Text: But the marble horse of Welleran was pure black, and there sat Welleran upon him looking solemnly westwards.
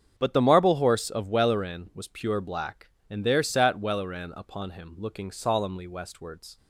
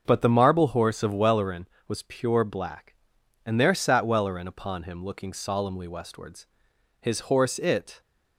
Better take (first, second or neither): first